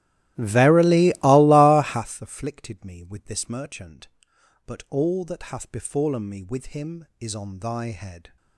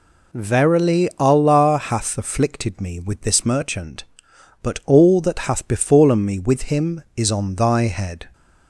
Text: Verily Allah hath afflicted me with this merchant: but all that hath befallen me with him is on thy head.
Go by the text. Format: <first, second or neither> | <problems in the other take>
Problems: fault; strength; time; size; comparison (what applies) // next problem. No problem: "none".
second | starts louder than the rest; strong; until 2.1 s; 15 dB